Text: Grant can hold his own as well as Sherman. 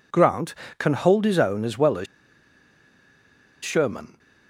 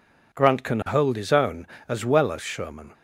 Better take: second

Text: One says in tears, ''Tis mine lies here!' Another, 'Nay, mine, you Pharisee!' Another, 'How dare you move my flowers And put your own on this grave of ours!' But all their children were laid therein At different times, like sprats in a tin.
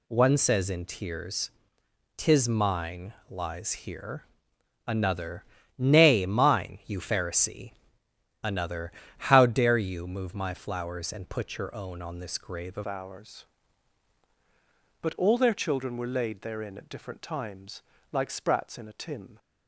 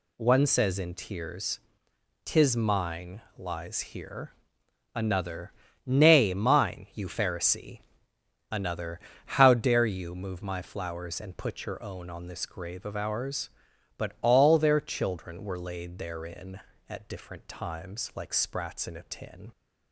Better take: second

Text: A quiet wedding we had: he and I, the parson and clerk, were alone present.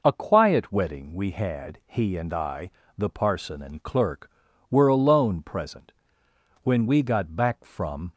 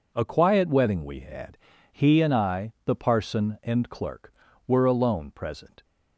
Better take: second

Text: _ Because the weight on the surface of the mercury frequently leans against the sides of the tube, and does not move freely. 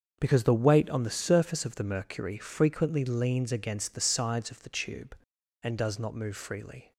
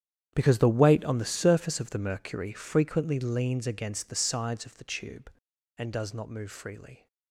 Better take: first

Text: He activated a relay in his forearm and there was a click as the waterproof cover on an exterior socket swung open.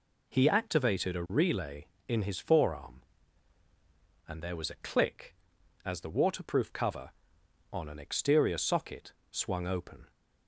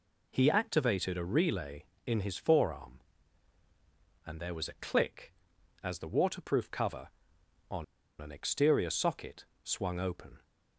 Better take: first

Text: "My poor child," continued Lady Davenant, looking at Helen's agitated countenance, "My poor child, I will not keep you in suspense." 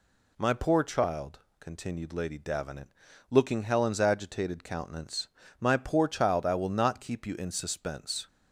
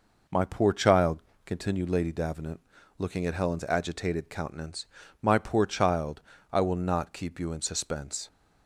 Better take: second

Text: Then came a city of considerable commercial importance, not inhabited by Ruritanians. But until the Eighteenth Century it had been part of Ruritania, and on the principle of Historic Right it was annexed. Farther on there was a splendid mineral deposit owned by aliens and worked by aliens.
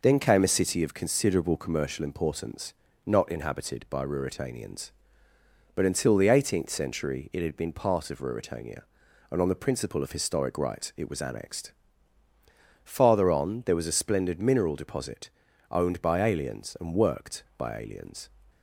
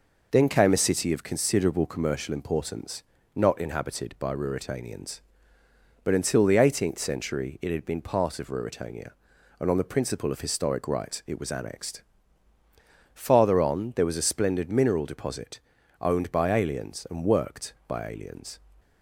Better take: neither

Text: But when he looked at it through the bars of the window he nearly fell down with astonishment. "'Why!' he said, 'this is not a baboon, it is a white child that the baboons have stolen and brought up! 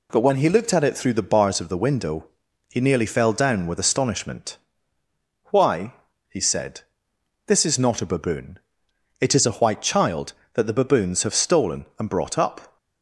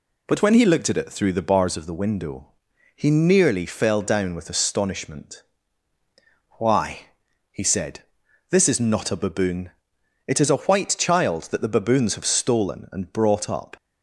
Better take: neither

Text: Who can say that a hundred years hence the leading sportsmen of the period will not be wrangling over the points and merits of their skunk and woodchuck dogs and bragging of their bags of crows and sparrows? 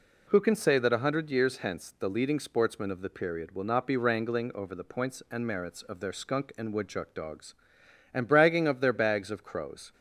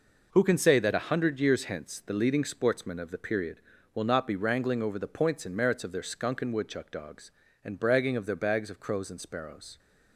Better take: second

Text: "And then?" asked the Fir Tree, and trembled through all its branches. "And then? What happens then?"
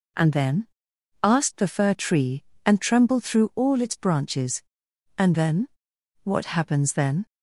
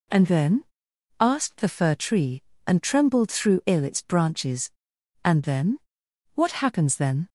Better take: first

